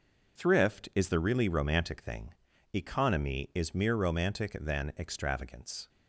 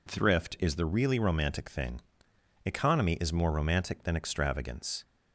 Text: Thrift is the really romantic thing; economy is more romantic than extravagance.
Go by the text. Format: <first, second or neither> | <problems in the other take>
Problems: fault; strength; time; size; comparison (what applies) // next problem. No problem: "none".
second | says "mere" for "more"; at 3.7 s